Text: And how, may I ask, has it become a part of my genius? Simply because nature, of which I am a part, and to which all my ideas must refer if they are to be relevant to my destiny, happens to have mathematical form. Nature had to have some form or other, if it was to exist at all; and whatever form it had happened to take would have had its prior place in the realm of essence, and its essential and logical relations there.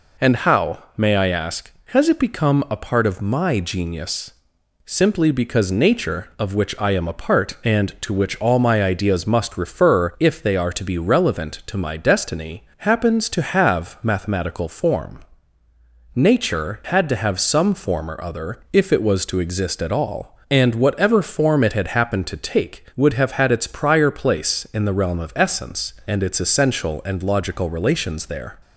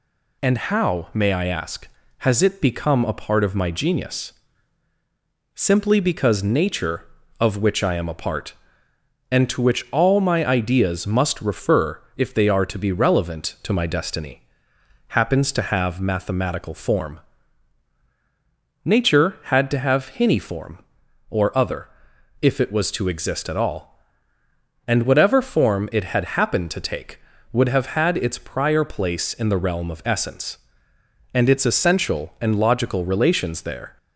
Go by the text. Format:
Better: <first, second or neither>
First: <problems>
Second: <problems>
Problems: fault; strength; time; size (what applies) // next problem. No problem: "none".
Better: first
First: none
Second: says "hinny" for "some"; at 20.0 s